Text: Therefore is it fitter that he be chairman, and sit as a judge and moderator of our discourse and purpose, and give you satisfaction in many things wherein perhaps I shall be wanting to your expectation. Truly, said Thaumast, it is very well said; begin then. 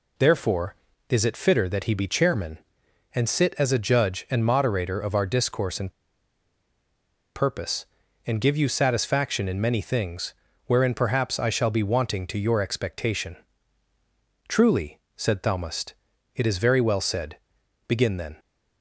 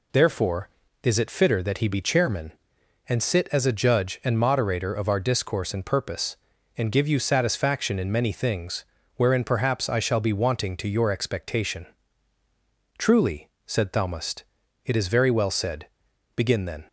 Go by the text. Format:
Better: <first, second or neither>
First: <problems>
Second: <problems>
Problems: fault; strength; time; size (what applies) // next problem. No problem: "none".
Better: second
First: pauses between "and" and "purpose"; strong; at 5.9 s; 1.4 s long // pauses between "things" and "wherein"; slight; at 10.3 s; 0.32 s long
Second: pauses between "things" and "wherein"; slight; at 8.8 s; 0.31 s long